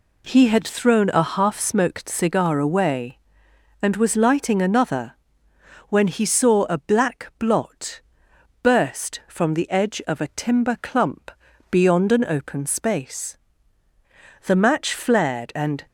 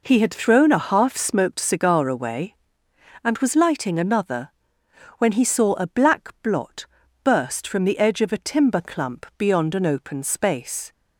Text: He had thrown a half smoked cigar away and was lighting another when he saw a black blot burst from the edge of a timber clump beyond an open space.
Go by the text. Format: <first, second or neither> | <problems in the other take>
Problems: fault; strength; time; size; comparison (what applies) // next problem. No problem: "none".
second | pauses between "another" and "when"; noticeable; at 5.1 s; 0.76 s long; noticeable in the second // pauses between "blot" and "burst"; noticeable; at 8.0 s; 0.62 s long; also in the second // pauses between "clump" and "beyond"; at 11.2 s; 0.40 s long // goes on to say "The match flared and"; from 14.4 s on; 1.4 s long